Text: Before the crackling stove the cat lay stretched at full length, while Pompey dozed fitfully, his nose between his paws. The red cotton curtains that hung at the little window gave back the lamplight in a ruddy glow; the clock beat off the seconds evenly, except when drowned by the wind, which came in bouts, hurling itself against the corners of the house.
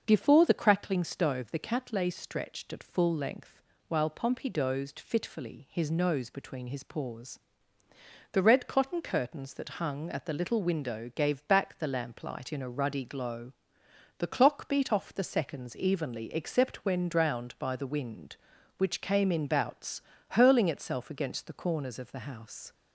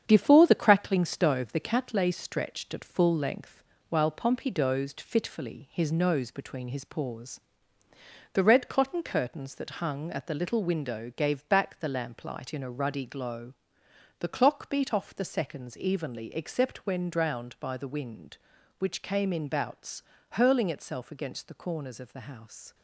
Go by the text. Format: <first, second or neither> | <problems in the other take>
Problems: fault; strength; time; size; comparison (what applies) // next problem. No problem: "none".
first | gets quieter; throughout; 6 dB // starts louder than the rest; strong; until 1.0 s; 8 dB; also in the first